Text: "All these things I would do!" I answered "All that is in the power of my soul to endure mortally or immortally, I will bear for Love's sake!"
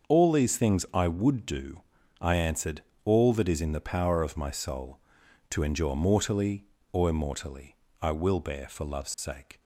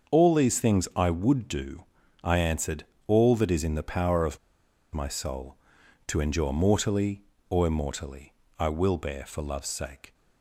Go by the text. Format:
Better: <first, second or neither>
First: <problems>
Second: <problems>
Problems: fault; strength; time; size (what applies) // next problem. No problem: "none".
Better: first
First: starts louder than the rest; until 1.1 s; 6.5 dB // pauses between "answered" and "All"; slight; at 2.8 s; 0.24 s long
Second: starts louder than the rest; until 1.1 s; 6.5 dB // pauses between "answered" and "All"; slight; at 2.8 s; 0.24 s long // pauses between "of" and "my"; noticeable; at 4.3 s; 0.55 s long